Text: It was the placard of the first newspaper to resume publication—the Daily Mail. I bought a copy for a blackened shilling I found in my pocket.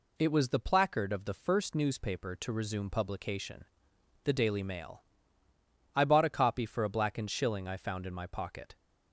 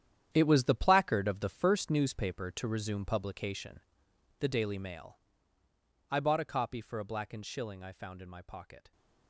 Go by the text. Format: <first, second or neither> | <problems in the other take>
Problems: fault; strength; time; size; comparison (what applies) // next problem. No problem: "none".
first | gets quieter; strong; throughout; 13 dB